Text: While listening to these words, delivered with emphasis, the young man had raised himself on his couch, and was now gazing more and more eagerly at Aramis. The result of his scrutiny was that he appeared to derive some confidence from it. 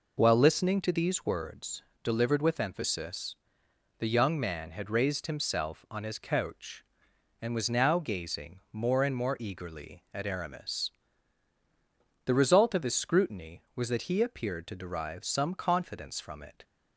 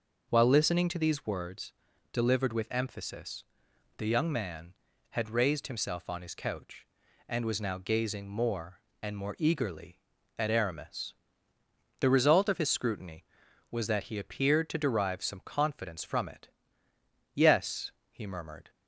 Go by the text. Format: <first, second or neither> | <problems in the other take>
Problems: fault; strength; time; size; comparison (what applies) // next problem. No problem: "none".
first | goes on to say "Yes he murmured"; from 17.3 s on; 1.3 s long